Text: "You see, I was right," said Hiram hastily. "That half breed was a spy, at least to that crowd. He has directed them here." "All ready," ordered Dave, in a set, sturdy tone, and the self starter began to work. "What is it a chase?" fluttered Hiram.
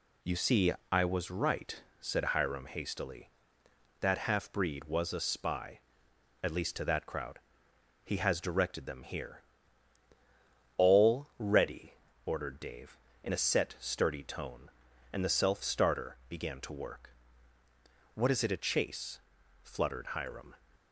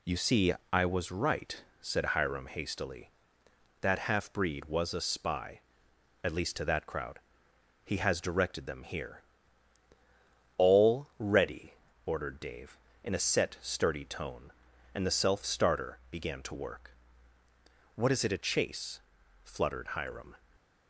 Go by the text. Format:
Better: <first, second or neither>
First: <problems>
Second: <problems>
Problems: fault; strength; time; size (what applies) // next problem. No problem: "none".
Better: neither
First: none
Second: none